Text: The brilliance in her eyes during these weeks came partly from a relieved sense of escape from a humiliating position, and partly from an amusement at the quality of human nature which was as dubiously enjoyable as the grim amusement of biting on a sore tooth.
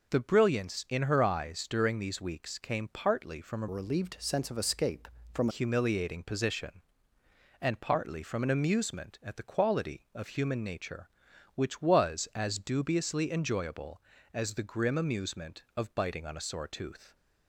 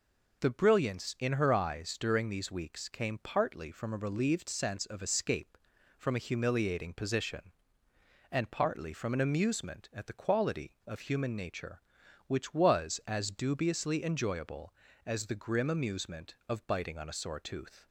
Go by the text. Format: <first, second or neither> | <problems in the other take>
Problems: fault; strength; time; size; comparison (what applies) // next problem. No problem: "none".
second | changes voice from "relieved" to "from"; from 3.6 to 5.4 s; 1.8 s long